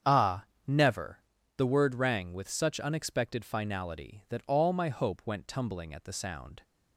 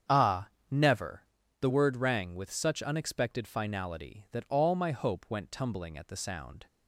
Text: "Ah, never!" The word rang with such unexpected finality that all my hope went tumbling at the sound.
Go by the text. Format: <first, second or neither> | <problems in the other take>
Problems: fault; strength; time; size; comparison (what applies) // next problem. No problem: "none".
neither | starts louder than the rest; strong; the same in both